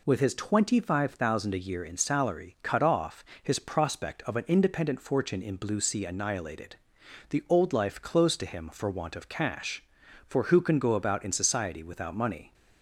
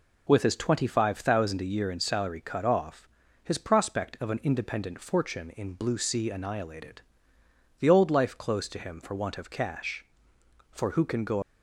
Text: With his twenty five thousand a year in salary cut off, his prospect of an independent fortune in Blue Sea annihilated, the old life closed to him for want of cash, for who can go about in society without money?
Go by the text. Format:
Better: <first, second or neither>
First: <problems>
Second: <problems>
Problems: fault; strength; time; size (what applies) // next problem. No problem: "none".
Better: first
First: none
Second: stops before "about in society without money"; at 11.4 s